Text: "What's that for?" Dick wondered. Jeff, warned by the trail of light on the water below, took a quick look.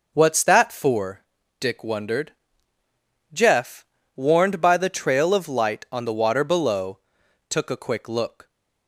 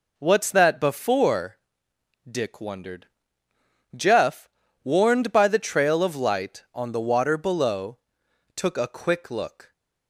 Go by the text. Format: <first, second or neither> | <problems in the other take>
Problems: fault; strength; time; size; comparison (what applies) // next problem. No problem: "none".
first | says "before" for "for"; at 0.7 s